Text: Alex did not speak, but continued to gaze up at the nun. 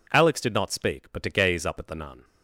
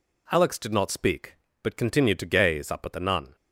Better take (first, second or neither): second